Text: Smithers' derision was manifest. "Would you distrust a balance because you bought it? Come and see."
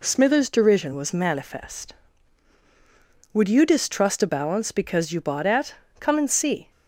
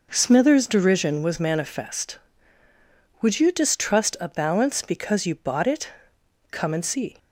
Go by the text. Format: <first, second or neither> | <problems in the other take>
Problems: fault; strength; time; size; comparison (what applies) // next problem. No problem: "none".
second | says "at" for "it"; at 5.4 s